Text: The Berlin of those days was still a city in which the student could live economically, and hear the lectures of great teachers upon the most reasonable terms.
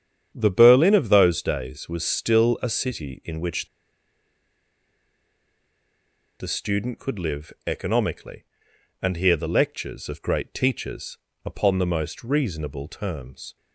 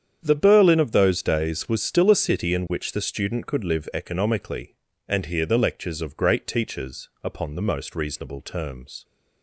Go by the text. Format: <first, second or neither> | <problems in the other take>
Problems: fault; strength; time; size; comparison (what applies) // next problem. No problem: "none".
second | starts louder than the rest; strong; until 1.3 s; 8.5 dB; strong in the second // pauses between "which" and "the"; strong; at 3.6 s; 2.7 s long // pauses between "teachers" and "upon"; slight; at 11.1 s; 0.26 s long